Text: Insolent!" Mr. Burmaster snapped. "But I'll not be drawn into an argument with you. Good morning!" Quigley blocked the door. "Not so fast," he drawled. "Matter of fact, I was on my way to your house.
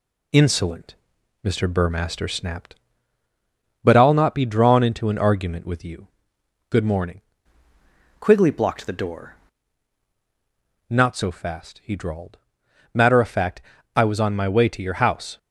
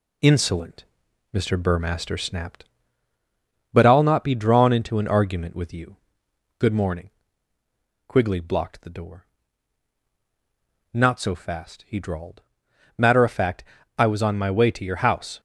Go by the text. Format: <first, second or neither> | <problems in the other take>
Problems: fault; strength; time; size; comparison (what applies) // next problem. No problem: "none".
second | changes voice from "Quigley" to "door"; from 8.1 to 9.3 s; 1.2 s long